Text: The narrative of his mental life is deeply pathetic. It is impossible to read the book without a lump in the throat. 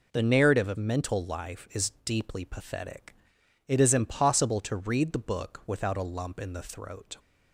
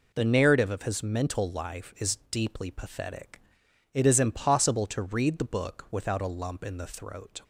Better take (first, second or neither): second